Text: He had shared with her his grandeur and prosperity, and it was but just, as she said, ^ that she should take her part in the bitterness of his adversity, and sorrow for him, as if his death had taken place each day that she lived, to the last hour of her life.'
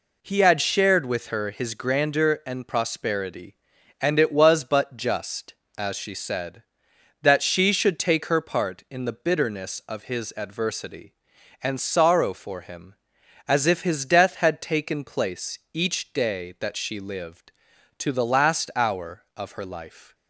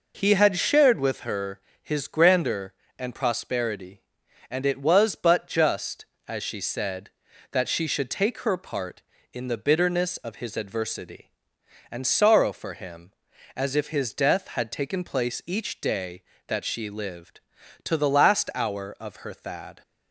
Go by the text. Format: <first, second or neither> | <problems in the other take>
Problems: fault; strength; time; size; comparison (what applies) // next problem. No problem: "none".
first | pauses between "her" and "his"; slight; at 1.5 s; 0.24 s long // says "thad" for "life"; at 19.3 s